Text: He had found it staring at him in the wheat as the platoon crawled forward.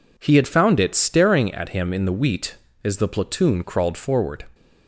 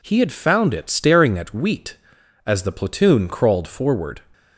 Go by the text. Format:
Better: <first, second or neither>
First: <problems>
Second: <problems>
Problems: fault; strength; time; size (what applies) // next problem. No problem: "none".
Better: first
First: none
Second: skips "him in the"; at 1.5 s